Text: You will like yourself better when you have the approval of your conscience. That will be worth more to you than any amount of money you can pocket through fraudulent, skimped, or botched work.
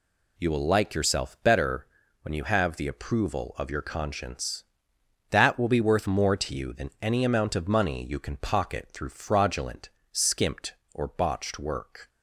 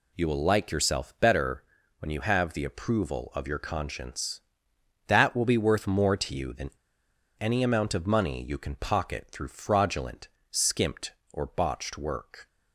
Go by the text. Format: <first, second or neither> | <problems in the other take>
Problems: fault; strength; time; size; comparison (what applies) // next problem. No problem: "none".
first | pauses between "better" and "when"; slight; at 1.6 s; 0.36 s long; slight in the first // pauses between "than" and "any"; noticeable; at 6.7 s; 0.68 s long